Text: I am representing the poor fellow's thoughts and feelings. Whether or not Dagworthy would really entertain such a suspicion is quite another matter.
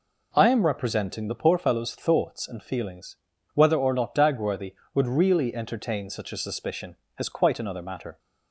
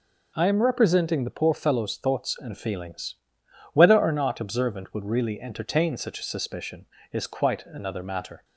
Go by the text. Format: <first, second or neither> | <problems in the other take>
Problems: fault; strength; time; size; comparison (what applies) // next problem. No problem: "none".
first | says "Observant" for "Dagworthy"; at 4.3 s